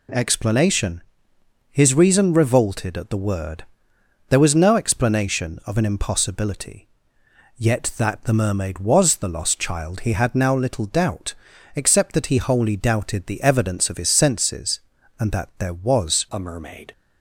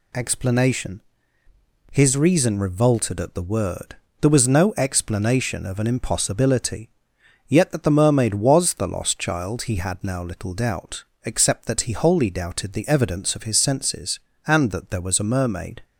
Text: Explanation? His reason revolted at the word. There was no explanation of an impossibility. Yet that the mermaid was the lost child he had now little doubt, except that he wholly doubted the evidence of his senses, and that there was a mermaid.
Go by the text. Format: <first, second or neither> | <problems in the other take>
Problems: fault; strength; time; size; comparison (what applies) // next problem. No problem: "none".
second | changes voice at "a"; from 16.2 s on; 0.7 s long